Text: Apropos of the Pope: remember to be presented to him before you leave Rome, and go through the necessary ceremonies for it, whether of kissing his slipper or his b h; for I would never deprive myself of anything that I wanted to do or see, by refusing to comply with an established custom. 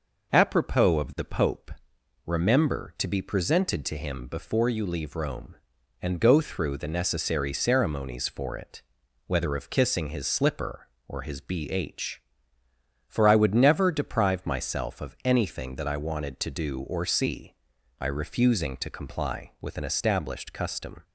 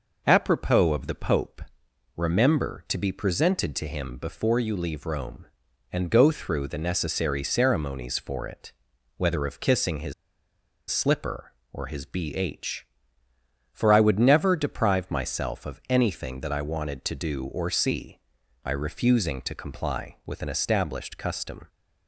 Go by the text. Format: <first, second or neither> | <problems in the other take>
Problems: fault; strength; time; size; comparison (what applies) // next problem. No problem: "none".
first | pauses between "his" and "slipper"; noticeable; at 10.1 s; 0.76 s long